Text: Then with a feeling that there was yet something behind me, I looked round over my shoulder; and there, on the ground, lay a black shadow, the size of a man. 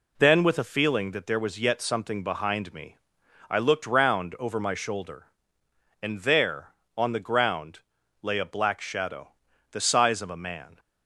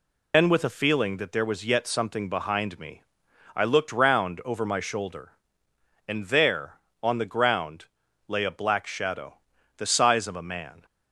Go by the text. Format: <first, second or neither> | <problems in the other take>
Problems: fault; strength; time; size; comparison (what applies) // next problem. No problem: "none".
first | loses the start of "Then"; at 0.3 s; 115 ms